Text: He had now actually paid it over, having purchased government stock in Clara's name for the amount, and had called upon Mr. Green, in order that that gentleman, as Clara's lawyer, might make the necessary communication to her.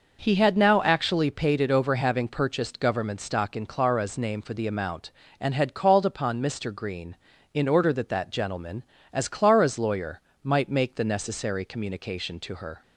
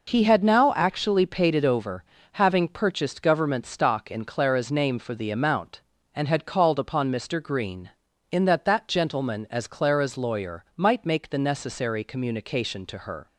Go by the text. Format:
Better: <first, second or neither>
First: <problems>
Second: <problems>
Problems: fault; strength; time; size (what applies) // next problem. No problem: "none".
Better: first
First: none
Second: skips "order"; at 8.4 s